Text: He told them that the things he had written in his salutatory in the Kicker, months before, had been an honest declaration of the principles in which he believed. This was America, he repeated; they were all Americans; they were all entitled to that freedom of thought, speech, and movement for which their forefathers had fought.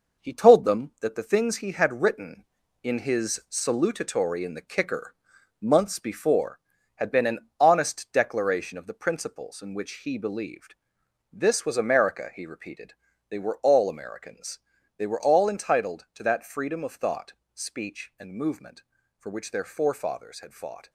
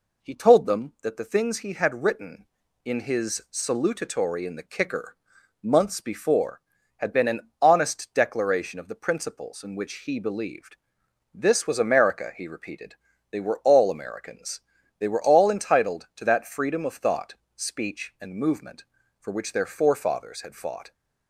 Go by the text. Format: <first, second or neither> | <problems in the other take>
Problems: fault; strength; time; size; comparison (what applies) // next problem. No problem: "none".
second | gets quieter; noticeable; throughout; 6 dB